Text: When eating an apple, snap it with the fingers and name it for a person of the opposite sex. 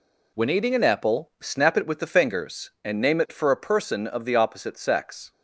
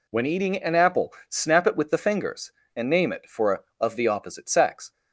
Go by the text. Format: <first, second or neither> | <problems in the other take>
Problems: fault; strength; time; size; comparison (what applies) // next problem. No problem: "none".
first | skips "person"; at 3.6 s